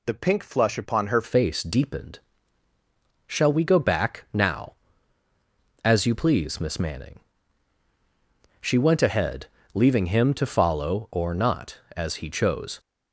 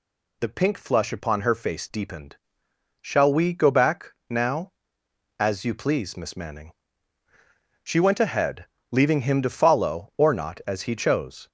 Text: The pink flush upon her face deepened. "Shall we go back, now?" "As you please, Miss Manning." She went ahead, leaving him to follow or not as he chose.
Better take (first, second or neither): second